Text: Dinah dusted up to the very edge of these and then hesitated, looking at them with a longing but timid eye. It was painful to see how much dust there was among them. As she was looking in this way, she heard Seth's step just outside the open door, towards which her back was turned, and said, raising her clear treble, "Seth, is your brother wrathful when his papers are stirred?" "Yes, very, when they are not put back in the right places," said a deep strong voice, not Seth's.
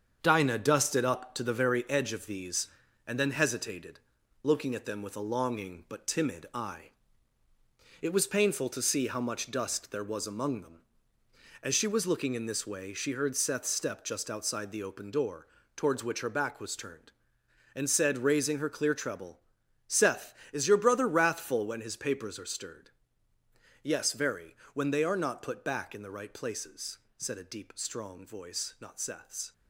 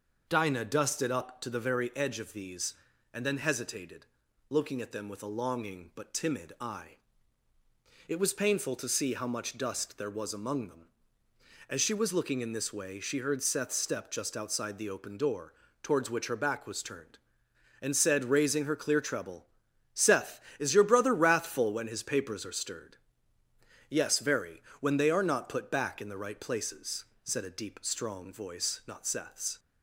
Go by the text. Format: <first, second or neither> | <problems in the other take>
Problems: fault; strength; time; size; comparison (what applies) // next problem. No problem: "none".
second | gets quieter; throughout; 6.5 dB